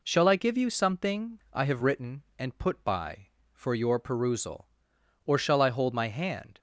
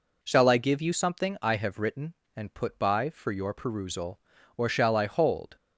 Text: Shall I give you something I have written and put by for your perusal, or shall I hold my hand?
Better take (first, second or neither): first